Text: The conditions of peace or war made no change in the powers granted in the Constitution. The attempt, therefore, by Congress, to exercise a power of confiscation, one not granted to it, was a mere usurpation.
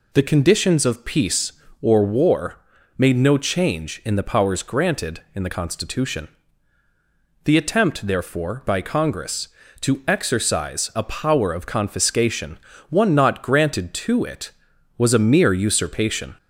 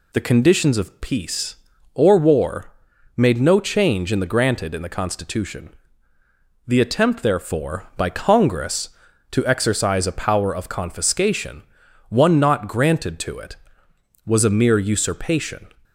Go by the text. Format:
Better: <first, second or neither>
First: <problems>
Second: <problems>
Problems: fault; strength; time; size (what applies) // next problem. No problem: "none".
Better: first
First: pauses between "war" and "made"; at 2.5 s; 0.38 s long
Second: pauses between "war" and "made"; at 2.7 s; 0.44 s long // skips "powers"; at 4.2 s